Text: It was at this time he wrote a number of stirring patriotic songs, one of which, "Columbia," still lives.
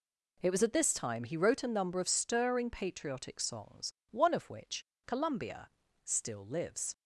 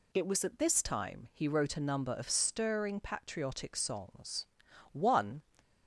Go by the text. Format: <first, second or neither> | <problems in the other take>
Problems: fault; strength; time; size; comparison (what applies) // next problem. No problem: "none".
first | stops before "of which Columbia still lives"; at 5.5 s